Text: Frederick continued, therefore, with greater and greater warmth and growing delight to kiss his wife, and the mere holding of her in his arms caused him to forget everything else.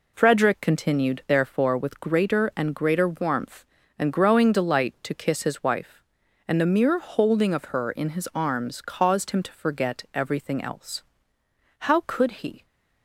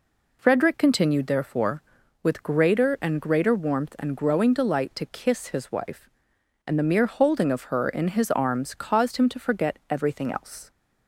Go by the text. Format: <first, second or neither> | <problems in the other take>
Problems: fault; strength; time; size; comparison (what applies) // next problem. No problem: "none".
second | goes on to say "How could he"; noticeable; from 11.7 s on; 0.86 s long